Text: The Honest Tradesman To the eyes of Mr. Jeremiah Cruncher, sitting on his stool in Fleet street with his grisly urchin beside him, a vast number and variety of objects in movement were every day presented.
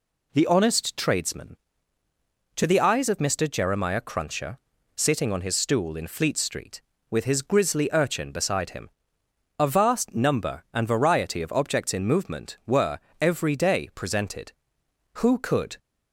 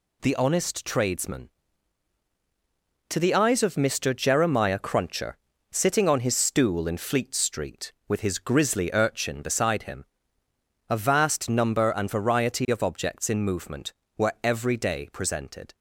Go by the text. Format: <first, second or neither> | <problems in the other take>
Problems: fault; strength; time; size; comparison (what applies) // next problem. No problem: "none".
second | pauses between "were" and "every"; slight; at 12.9 s; 0.24 s long // goes on to say "Who could"; noticeable; from 15.1 s on; 0.64 s long